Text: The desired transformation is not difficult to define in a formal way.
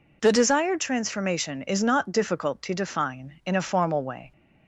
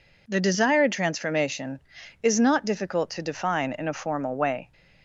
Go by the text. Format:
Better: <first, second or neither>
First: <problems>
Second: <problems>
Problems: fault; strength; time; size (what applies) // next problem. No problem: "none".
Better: neither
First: none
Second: none